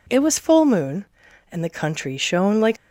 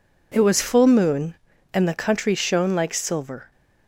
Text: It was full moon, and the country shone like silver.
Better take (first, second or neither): second